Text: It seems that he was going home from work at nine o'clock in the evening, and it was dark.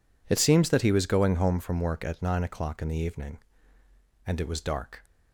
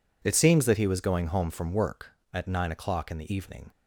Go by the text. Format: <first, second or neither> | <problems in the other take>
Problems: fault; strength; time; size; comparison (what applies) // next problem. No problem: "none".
first | stops before "and it was dark"; at 3.7 s